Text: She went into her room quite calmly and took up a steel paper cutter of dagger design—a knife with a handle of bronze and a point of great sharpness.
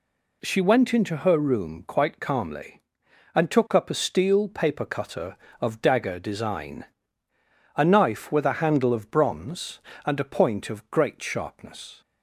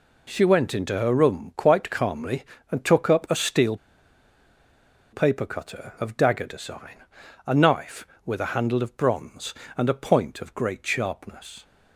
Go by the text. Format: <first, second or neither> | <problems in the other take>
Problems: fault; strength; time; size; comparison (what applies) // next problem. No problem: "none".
first | pauses between "steel" and "paper"; strong; at 3.7 s; 1.3 s long